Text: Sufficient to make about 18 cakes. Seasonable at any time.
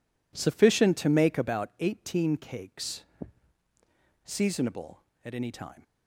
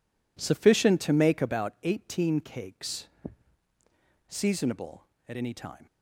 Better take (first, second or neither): neither